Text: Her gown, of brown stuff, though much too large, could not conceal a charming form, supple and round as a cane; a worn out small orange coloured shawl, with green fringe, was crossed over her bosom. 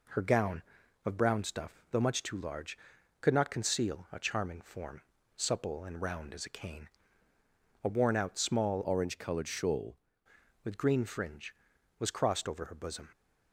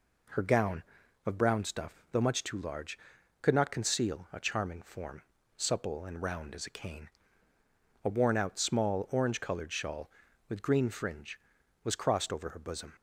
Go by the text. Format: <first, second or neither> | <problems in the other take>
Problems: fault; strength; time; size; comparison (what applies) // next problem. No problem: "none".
second | changes voice from "orange" to "shawl"; from 8.8 to 9.9 s; 1.1 s long